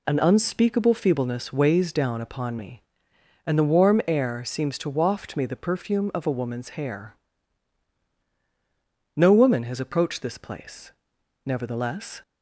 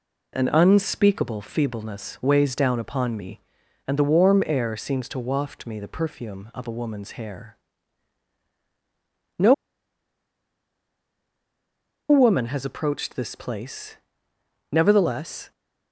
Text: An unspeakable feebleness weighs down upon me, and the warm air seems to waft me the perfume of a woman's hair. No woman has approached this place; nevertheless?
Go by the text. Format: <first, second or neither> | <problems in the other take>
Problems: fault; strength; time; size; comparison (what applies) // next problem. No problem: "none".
first | pauses between "No" and "woman"; strong; at 9.5 s; 2.5 s long